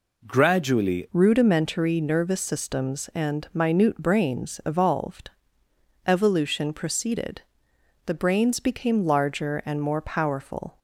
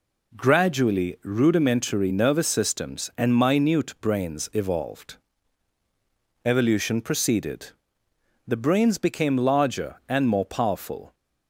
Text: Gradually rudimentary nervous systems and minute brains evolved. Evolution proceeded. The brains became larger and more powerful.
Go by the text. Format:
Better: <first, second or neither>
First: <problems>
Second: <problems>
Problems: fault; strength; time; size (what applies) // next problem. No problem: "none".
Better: second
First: changes voice at "rudimentary"; from 1.1 s on; 9.6 s long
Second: none